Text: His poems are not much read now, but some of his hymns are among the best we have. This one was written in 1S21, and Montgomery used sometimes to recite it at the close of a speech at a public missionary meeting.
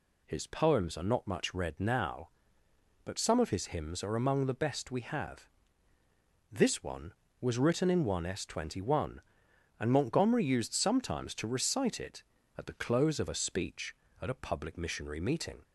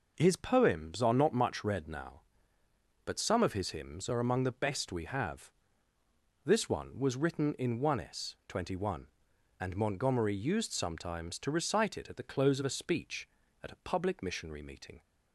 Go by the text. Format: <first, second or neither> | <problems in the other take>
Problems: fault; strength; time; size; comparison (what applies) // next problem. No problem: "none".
neither | none